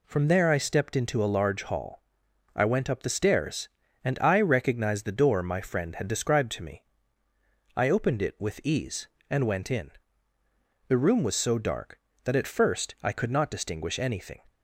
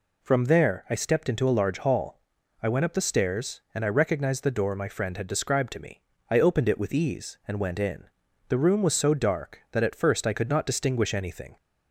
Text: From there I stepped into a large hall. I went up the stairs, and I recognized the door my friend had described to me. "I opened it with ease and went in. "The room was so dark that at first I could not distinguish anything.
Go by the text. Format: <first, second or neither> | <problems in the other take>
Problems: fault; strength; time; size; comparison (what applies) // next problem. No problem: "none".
neither | none